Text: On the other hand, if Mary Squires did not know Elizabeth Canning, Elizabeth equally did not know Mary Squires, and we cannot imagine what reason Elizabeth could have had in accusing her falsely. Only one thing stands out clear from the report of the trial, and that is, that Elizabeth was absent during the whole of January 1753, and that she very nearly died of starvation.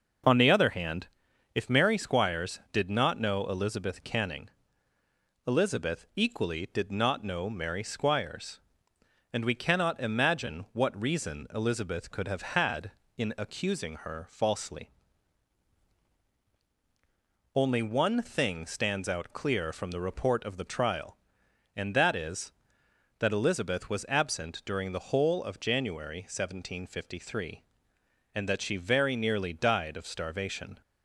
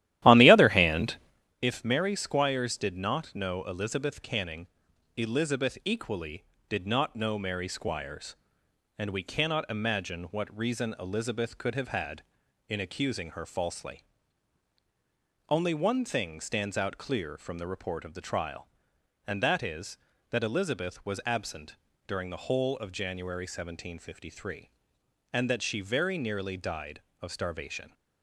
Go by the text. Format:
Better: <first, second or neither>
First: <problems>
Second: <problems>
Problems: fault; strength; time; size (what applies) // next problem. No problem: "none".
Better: first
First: none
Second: starts louder than the rest; strong; until 1.6 s; 13.5 dB // pauses between "absent" and "during"; slight; at 21.7 s; 0.32 s long